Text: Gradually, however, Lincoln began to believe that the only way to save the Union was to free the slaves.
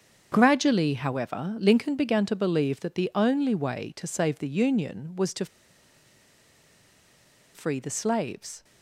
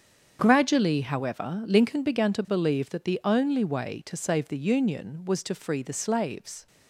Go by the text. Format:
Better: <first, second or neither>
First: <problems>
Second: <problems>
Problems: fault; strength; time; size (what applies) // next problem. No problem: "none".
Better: second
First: starts louder than the rest; strong; until 1.3 s; 7 dB // pauses between "to" and "free"; strong; at 5.4 s; 2.0 s long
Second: starts louder than the rest; strong; until 1.4 s; 7.5 dB